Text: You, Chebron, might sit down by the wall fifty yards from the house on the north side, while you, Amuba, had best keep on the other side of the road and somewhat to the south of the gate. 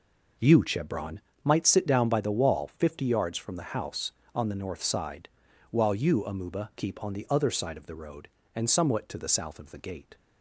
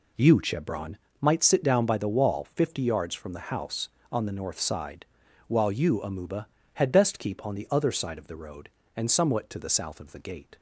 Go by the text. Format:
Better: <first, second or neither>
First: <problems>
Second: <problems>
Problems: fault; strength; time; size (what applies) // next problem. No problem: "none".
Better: second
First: skips "had best"; at 6.7 s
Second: none